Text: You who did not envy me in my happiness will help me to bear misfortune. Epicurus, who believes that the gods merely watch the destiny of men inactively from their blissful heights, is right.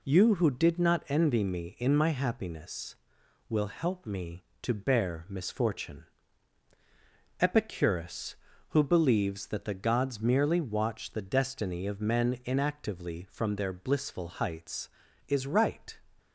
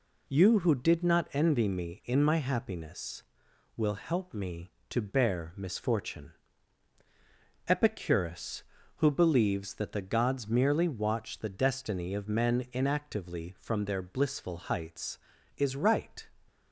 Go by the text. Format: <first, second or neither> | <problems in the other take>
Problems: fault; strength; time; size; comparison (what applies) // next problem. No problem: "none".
neither | none